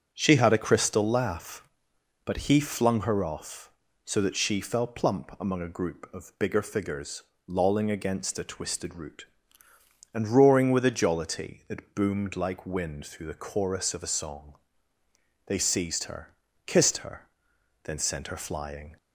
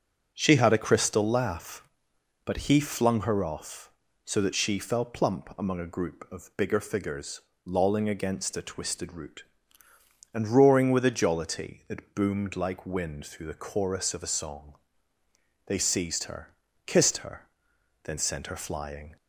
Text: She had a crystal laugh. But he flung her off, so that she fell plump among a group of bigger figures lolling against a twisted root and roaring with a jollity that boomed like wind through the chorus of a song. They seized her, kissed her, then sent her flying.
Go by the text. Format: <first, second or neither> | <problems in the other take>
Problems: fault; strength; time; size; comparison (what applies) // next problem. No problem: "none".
neither | pauses between "figures" and "lolling"; slight; the same in both